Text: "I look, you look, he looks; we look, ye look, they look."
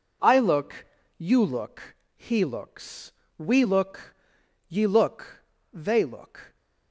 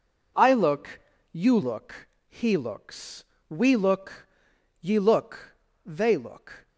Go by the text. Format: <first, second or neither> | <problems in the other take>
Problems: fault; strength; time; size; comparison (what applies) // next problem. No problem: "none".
neither | none